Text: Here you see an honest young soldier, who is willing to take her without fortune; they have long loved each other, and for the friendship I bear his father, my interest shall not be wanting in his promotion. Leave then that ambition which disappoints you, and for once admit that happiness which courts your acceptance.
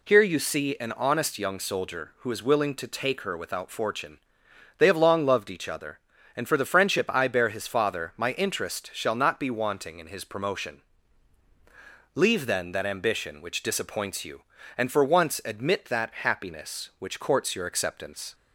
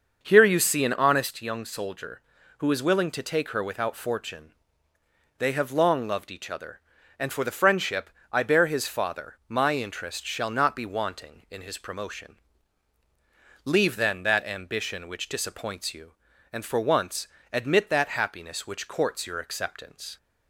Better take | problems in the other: first | starts louder than the rest; until 1.3 s; 6.5 dB // pauses between "friendship" and "I"; slight; at 8.0 s; 0.24 s long // pauses between "once" and "admit"; slight; at 17.2 s; 0.24 s long

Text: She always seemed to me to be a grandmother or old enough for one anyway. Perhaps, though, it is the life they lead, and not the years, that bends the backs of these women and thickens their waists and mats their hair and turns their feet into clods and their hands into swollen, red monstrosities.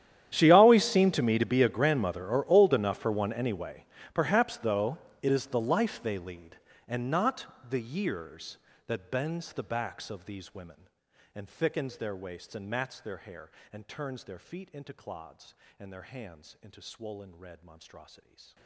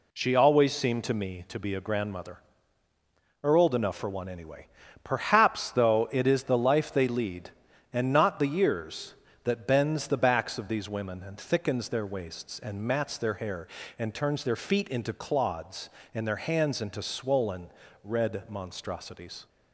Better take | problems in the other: second | gets quieter; strong; throughout; 24.5 dB // pauses between "not" and "the"; slight; at 7.4 s; 0.22 s long

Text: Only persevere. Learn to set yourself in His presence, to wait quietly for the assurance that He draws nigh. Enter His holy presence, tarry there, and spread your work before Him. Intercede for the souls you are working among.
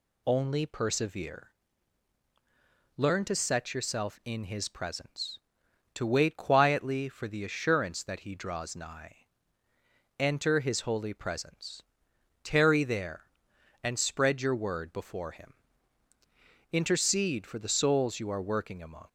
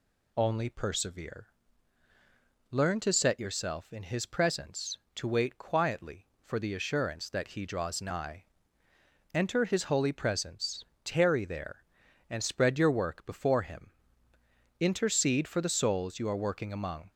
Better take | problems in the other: second | says "word" for "work"; at 14.5 s

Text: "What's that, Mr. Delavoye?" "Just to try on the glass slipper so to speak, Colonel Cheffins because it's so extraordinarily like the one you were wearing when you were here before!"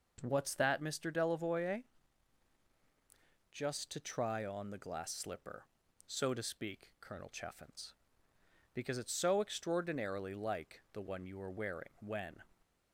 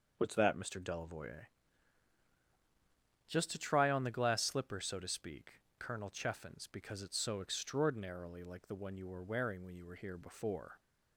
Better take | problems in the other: second | stops before "you were here before"; at 12.6 s

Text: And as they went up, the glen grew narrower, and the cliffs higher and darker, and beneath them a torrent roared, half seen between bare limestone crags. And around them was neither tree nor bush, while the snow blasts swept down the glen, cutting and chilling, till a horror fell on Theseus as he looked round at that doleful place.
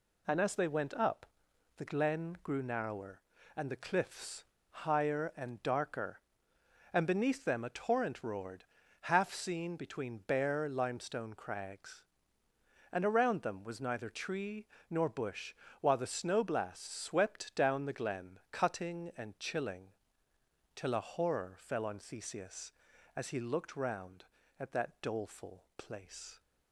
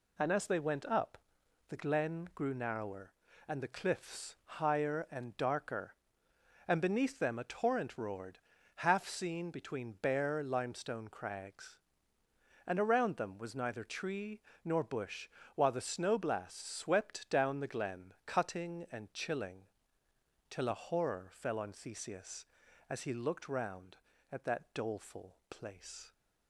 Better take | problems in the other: second | pauses between "cliffs" and "higher"; slight; at 4.4 s; 0.27 s long // pauses between "tree" and "nor"; slight; at 14.6 s; 0.24 s long; slight in the second

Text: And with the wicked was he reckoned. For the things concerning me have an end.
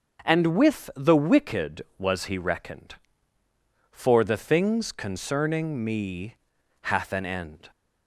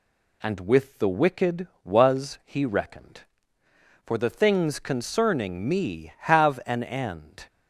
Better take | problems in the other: second | starts louder than the rest; until 1.3 s; 6 dB // says "hath" for "have"; at 6.8 s

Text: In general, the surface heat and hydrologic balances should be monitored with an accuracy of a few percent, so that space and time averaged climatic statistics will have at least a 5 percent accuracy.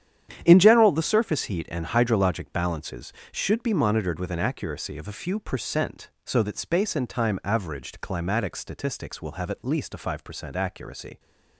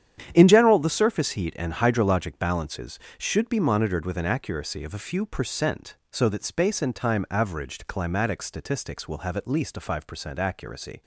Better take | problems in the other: neither | starts louder than the rest; strong; the same in both

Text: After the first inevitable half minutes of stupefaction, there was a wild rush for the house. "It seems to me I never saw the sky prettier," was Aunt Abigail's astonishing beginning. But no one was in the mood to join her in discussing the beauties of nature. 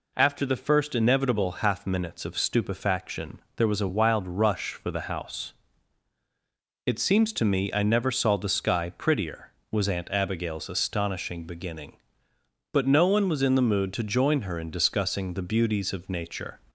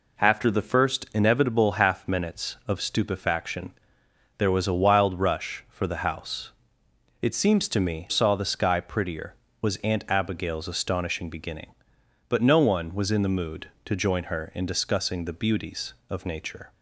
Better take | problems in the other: first | skips "I never"; at 8.0 s

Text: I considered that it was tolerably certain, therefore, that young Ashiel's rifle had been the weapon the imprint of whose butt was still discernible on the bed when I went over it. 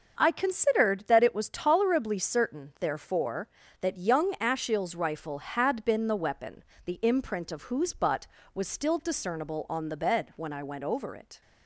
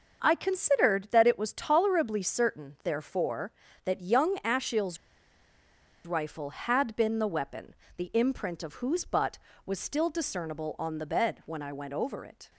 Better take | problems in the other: first | starts louder than the rest; until 1.2 s; 6.5 dB; also in the first // pauses between "Ashiel's" and "rifle"; at 4.9 s; 1.0 s long // pauses between "weapon" and "the"; slight; at 7.7 s; 0.24 s long; slight in the first

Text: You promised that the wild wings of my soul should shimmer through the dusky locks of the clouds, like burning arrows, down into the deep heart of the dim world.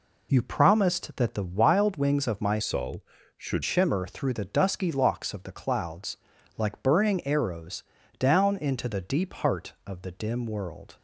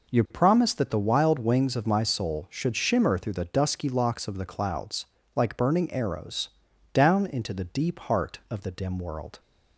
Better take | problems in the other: second | changes voice from "soul" to "should"; from 2.6 to 3.6 s; 1.0 s long

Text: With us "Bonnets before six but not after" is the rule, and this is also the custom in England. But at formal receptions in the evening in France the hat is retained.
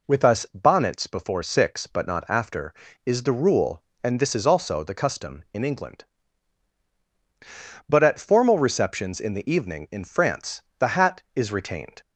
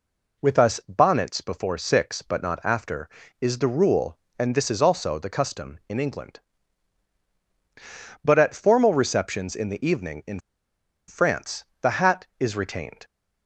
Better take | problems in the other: first | pauses between "in" and "France"; noticeable; at 10.3 s; 0.70 s long // pauses between "France" and "the"; slight; at 11.6 s; 0.16 s long; slight in the first

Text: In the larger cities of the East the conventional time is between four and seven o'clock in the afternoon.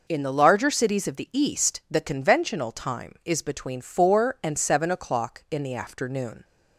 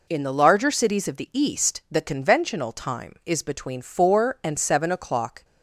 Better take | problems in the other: first | stops before "in the afternoon"; at 5.4 s

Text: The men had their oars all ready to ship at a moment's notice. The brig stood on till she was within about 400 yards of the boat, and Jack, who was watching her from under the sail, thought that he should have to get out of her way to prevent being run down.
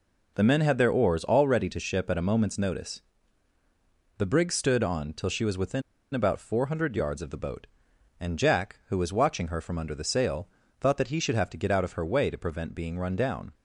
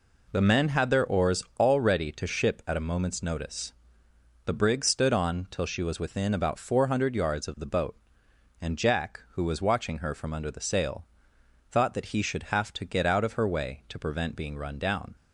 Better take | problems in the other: second | pauses between "within" and "about"; slight; at 5.8 s; 0.31 s long

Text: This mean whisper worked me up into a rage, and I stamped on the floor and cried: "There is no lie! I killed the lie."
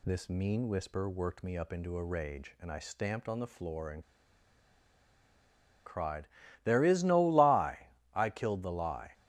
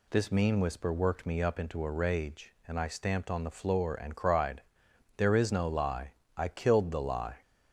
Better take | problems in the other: second | pauses between "and" and "cried"; strong; at 4.0 s; 1.8 s long

